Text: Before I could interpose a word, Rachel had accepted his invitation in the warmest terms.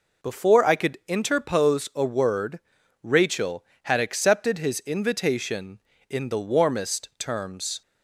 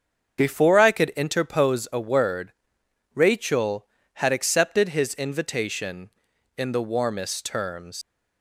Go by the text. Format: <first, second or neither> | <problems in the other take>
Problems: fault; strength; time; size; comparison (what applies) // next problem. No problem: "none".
first | starts louder than the rest; strong; until 1.4 s; 7.5 dB // leaves "terms" unfinished; at 8.0 s; 120 ms